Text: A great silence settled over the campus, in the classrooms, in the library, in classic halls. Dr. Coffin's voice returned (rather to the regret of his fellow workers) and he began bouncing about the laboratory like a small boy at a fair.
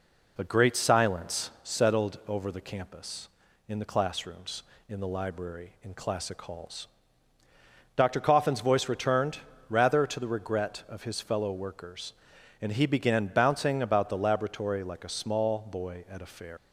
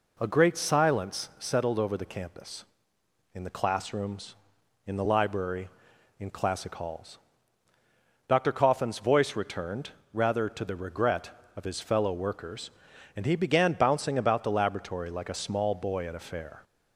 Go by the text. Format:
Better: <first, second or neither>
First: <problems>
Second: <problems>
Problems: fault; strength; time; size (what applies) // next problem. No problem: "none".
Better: second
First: leaves "fair" unfinished; at 16.5 s; 85 ms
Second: none